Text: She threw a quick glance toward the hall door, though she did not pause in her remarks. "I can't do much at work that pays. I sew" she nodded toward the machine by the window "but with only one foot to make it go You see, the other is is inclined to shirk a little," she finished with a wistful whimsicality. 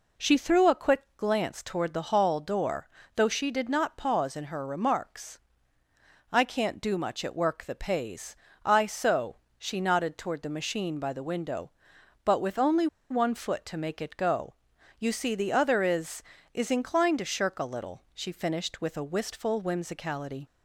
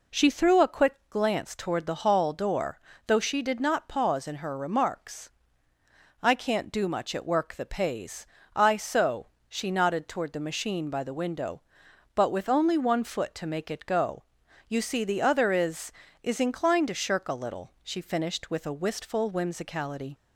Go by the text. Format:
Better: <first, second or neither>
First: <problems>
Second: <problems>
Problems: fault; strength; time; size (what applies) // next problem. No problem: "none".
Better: second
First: pauses between "sew" and "she"; slight; at 9.3 s; 0.22 s long // pauses between "only" and "one"; slight; at 12.8 s; 0.24 s long // pauses between "go" and "You"; noticeable; at 14.5 s; 0.46 s long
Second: pauses between "sew" and "she"; slight; at 9.2 s; 0.22 s long // pauses between "go" and "You"; noticeable; at 14.2 s; 0.46 s long